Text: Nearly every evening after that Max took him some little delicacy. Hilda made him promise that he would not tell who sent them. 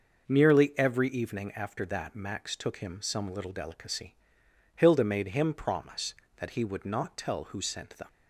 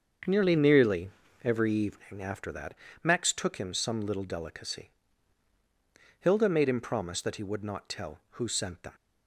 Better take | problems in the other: first | starts louder than the rest; until 1.6 s; 7 dB // says "Nearly" twice; at 0.5 s // pauses between "that" and "Max"; slight; at 2.7 s; 0.28 s long

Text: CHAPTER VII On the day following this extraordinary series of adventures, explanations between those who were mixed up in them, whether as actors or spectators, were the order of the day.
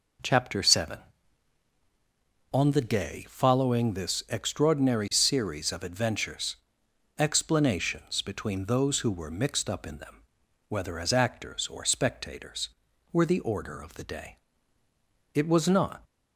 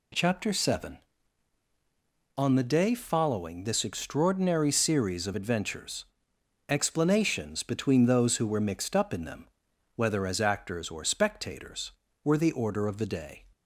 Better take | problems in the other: second | goes on to say "It was not"; noticeable; from 15.3 s on; 0.68 s long

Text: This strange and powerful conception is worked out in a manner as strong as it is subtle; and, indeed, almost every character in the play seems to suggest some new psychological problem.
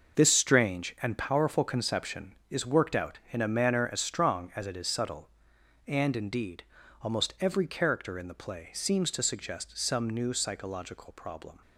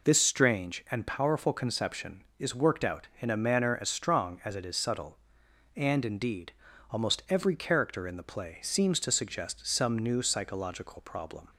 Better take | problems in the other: second | gets quieter; strong; throughout; 9.5 dB

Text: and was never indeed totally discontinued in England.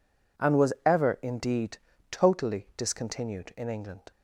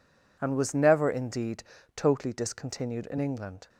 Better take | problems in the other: second | says "ever" for "never"; at 0.8 s // pauses between "indeed" and "totally"; slight; at 1.7 s; 0.32 s long; slight in the second

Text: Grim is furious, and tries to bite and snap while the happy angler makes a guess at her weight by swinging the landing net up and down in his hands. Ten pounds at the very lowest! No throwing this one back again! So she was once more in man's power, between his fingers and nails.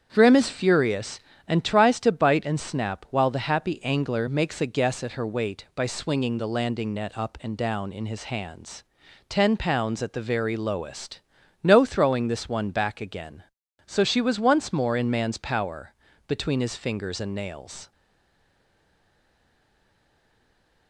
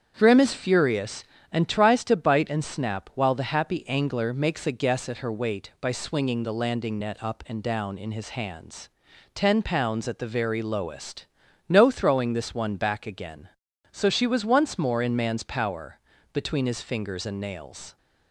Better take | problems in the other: second | starts louder than the rest; strong; until 1.1 s; 8 dB; strong in the second // stays silent after the last word; strong; from 17.9 s on; 2.9 s long

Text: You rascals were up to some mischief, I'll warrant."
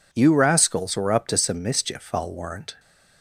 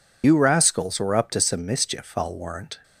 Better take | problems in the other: first | loses the start of "You"; at 0.2 s; 75 ms

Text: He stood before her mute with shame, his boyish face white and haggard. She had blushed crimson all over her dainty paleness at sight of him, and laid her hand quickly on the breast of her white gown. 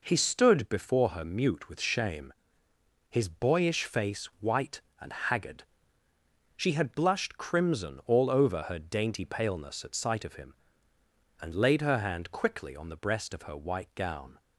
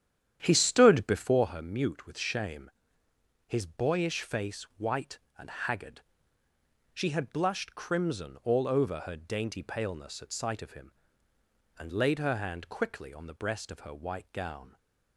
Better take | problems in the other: first | starts louder than the rest; strong; until 1.6 s; 10 dB

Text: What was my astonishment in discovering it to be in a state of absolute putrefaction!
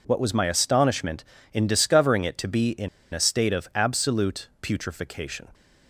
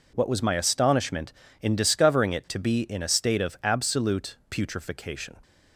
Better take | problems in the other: second | pauses between "in" and "a"; slight; at 2.8 s; 0.25 s long

